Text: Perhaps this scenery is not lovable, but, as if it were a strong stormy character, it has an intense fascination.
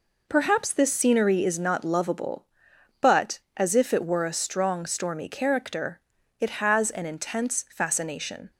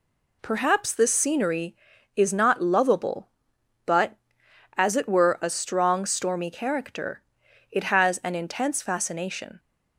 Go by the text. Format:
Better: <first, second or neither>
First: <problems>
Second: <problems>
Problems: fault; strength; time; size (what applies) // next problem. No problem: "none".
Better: first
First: none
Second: skips "if"; at 4.9 s